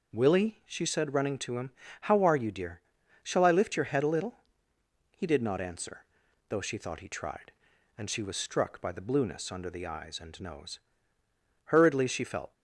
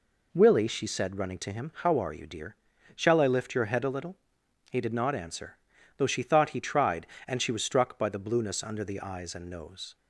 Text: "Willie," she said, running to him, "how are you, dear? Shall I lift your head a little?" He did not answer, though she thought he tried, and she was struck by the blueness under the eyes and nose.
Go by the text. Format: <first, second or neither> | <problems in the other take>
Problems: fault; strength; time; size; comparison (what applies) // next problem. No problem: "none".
second | goes on to say "Hurriedly she felt"; noticeable; from 11.6 s on; 0.88 s long